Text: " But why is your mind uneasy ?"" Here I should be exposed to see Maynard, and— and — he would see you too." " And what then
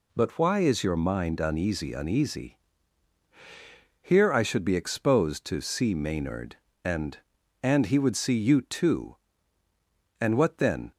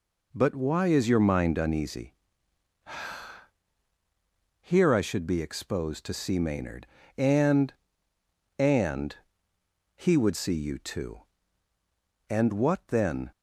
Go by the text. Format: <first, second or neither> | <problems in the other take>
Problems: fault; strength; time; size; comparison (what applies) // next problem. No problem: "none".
second | says "uneasy" twice; at 1.9 s